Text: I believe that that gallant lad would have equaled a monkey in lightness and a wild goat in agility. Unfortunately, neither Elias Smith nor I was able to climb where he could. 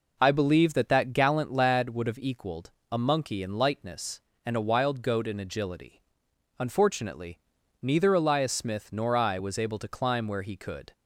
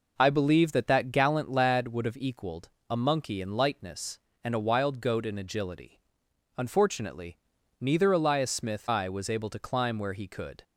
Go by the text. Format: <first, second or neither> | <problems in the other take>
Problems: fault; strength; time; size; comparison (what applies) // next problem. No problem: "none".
first | pauses between "equaled" and "a"; slight; at 2.6 s; 0.18 s long; slight in the first // skips "nor"; at 8.8 s